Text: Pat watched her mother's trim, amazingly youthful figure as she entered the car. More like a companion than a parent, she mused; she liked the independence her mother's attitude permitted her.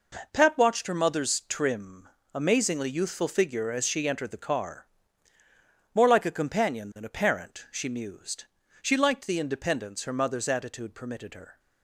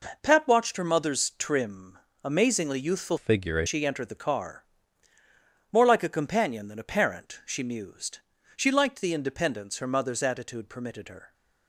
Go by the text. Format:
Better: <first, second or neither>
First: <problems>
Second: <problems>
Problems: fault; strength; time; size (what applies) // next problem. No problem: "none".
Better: first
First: none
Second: changes voice from "figure" to "as"; from 3.1 to 3.6 s; 0.5 s long